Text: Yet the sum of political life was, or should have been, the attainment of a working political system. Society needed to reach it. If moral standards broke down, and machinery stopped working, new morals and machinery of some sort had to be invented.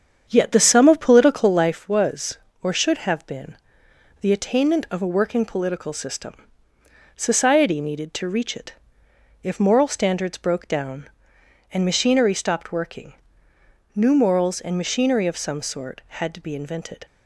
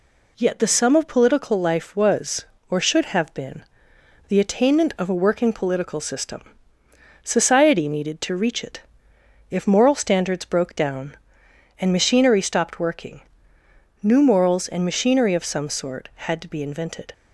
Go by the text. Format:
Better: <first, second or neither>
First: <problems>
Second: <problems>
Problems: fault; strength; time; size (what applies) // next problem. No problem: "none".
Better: second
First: starts louder than the rest; strong; until 1.8 s; 8 dB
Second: none